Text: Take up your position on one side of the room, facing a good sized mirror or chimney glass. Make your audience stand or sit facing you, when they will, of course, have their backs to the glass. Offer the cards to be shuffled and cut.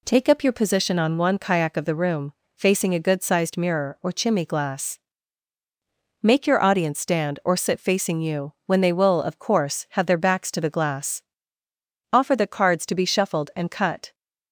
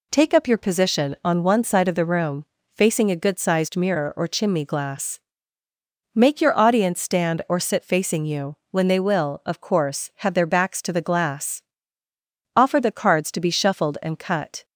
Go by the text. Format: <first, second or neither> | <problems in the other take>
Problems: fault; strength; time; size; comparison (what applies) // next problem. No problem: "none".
second | says "kayak" for "side"; at 1.3 s